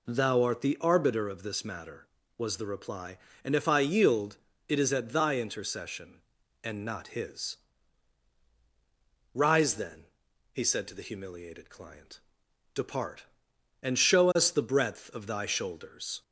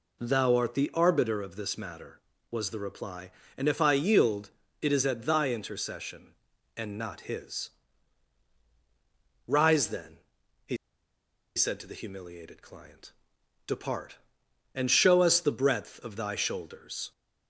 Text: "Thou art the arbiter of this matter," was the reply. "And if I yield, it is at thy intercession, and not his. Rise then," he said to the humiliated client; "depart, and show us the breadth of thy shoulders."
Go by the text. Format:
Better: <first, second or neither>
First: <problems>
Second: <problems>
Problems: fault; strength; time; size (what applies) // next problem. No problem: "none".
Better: first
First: none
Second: pauses between "he" and "said"; noticeable; at 10.7 s; 0.79 s long